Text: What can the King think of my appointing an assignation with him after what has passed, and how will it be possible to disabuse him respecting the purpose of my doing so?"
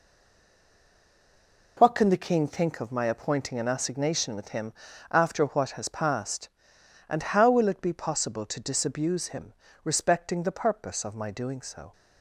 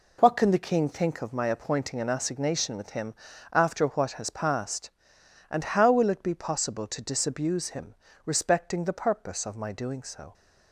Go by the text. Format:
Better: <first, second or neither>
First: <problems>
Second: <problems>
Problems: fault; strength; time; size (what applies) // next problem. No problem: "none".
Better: second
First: stays silent before the first word; noticeable; until 1.7 s; 1.7 s long // pauses between "him" and "after"; at 4.7 s; 0.40 s long // pauses between "him" and "respecting"; slight; at 9.5 s; 0.30 s long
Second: pauses between "him" and "after"; at 3.1 s; 0.40 s long // pauses between "him" and "respecting"; slight; at 7.9 s; 0.30 s long